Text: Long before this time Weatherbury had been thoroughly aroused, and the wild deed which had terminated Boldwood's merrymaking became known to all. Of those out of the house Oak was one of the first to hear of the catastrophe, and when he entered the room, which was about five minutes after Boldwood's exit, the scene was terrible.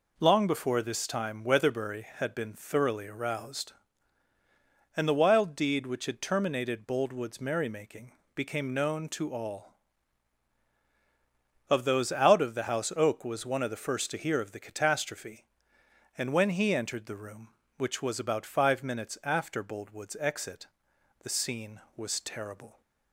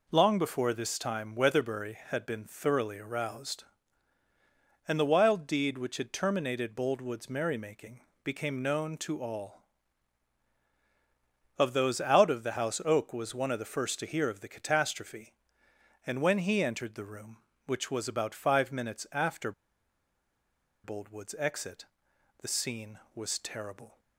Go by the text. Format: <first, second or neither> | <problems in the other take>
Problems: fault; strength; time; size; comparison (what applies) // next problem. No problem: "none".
first | pauses between "merrymaking" and "became"; slight; at 7.9 s; 0.24 s long; slight in the first // pauses between "after" and "Boldwood's"; strong; at 19.5 s; 1.3 s long